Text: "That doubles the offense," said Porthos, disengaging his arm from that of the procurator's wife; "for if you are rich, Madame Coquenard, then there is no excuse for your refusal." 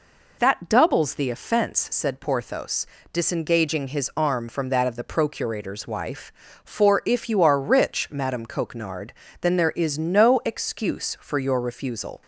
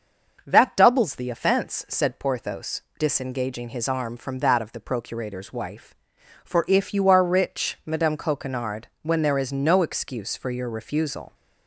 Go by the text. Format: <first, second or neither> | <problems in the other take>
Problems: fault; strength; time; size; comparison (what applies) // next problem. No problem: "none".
first | starts louder than the rest; until 1.4 s; 6 dB // says "when" for "then"; at 9.0 s